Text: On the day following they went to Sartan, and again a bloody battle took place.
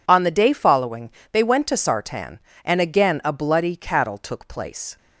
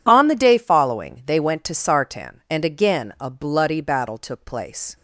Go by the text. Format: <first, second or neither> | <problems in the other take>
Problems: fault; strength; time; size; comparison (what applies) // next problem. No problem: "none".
second | pauses between "following" and "they"; slight; at 1.1 s; 0.20 s long // says "cattle" for "battle"; at 3.7 s